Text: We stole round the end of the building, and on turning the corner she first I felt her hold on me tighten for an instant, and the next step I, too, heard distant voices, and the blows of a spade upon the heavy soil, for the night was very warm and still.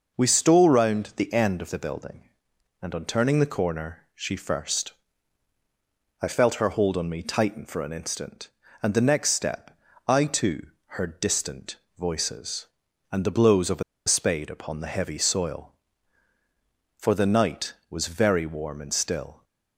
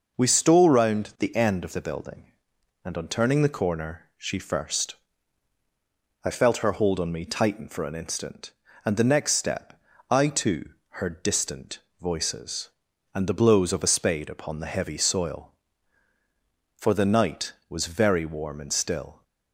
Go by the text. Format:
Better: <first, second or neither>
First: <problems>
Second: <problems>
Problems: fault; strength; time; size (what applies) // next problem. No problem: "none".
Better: second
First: pauses between "first" and "I"; strong; at 4.9 s; 1.3 s long // pauses between "step" and "I"; slight; at 9.7 s; 0.30 s long // pauses between "distant" and "voices"; slight; at 11.7 s; 0.20 s long // pauses between "a" and "spade"; slight; at 13.8 s; 0.24 s long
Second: pauses between "first" and "I"; strong; at 4.9 s; 1.3 s long // pauses between "step" and "I"; slight; at 9.7 s; 0.30 s long // pauses between "distant" and "voices"; slight; at 11.8 s; 0.20 s long